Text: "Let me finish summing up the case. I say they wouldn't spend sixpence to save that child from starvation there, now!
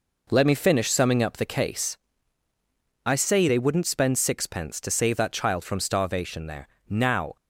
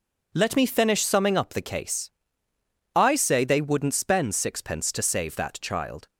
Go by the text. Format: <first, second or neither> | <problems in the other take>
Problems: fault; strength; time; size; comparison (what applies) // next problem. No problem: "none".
first | stops before "from starvation there now"; at 6.0 s